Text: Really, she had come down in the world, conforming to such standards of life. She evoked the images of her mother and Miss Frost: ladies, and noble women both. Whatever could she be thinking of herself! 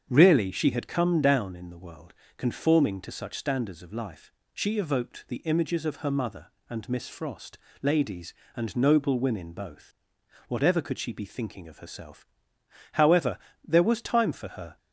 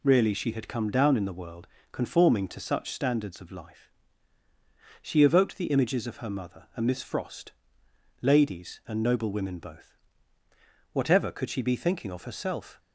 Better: second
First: starts louder than the rest; strong; until 1.0 s; 7.5 dB // goes on to say "However there was time for her"; strong; from 12.9 s on; 1.8 s long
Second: none

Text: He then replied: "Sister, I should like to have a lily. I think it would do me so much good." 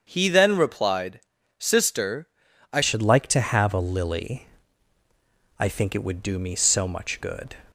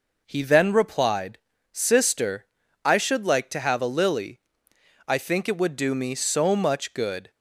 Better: second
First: starts louder than the rest; until 1.1 s; 7 dB // changes voice at "should"; from 2.8 s on; 4.7 s long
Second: none

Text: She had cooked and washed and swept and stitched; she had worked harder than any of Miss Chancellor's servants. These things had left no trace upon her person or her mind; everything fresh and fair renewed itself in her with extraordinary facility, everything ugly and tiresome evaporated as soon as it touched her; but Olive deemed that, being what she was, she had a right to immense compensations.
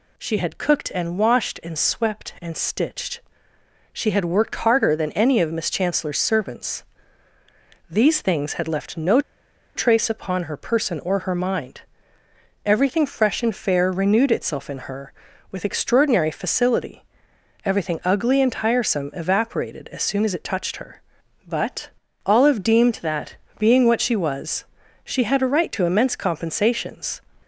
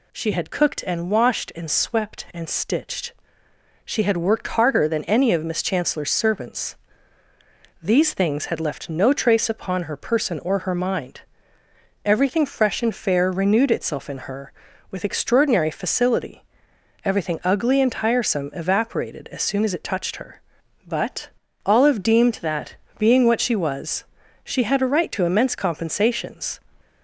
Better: second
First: pauses between "no" and "trace"; noticeable; at 9.1 s; 0.55 s long // pauses between "but" and "Olive"; at 21.8 s; 0.38 s long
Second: pauses between "but" and "Olive"; at 21.2 s; 0.38 s long

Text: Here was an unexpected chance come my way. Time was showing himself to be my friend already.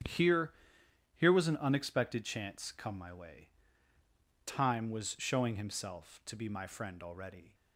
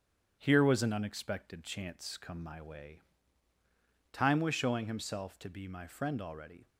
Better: second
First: starts louder than the rest; strong; until 1.7 s; 9.5 dB // says "Here" twice; at 1.1 s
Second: starts louder than the rest; strong; until 1.4 s; 7.5 dB

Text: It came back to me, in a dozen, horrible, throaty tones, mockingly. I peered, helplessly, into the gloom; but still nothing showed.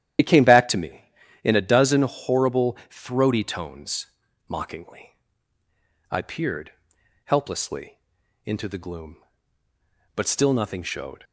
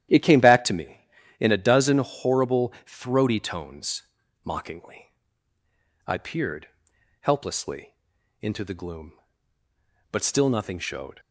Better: second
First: loses the start of "It"; at 0.1 s; 55 ms // starts louder than the rest; strong; until 1.6 s; 11 dB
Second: starts louder than the rest; strong; until 1.5 s; 11.5 dB

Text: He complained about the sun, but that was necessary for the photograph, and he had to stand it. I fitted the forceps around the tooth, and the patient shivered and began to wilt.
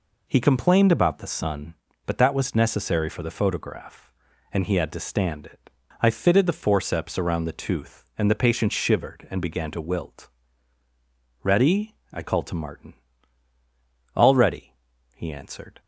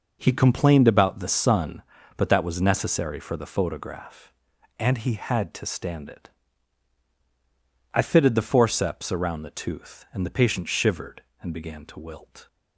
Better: second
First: goes on to say "Ready I called to Martin All ready he answered"; strong; from 11.4 s on; 4.3 s long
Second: none

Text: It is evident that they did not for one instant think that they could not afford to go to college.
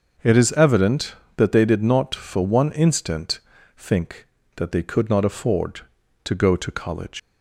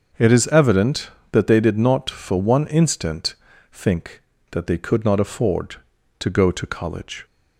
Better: second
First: starts louder than the rest; until 1.4 s; 6.5 dB // pauses between "instant" and "think"; at 3.3 s; 0.38 s long // leaves "college" unfinished; at 7.1 s; 100 ms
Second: starts louder than the rest; until 1.4 s; 6.5 dB // pauses between "instant" and "think"; at 3.3 s; 0.38 s long

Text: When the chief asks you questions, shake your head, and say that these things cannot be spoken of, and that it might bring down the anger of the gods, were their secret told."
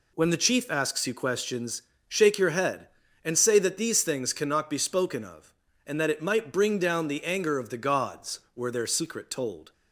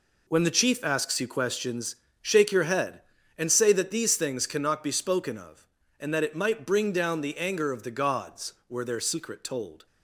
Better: first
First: none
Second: gets quieter; strong; throughout; 9.5 dB

